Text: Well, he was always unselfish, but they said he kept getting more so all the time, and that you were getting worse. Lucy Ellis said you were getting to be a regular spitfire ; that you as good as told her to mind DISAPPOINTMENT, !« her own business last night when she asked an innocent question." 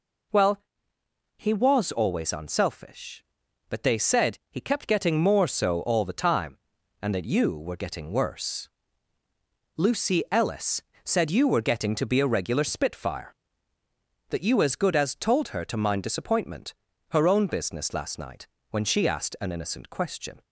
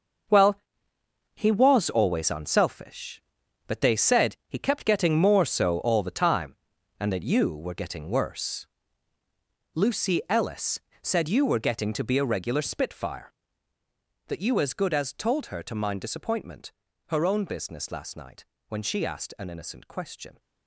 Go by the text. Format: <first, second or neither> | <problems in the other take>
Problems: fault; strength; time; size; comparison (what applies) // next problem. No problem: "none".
first | gets quieter; strong; throughout; 13 dB // pauses between "Ellis" and "said"; slight; at 10.7 s; 0.22 s long; slight in the first // pauses between "night" and "when"; slight; at 18.4 s; 0.24 s long; slight in the first